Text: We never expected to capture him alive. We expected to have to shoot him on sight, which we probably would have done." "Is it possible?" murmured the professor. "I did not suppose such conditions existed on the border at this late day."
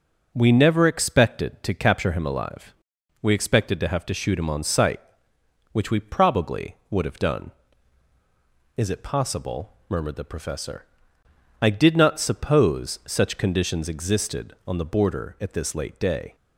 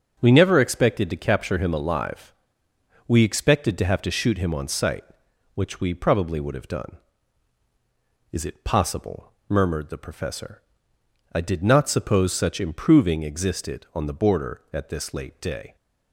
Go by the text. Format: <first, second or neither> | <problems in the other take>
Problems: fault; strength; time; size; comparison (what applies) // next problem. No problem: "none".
first | starts louder than the rest; strong; until 1.2 s; 7.5 dB // says "improving" for "conditions"; at 12.5 s